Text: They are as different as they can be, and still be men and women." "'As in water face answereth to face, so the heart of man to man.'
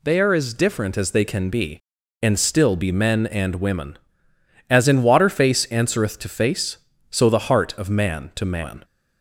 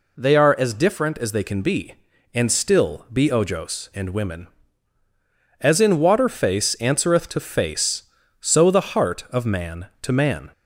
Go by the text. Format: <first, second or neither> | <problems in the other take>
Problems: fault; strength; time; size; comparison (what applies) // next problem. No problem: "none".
first | says "ojos" for "men"; at 3.2 s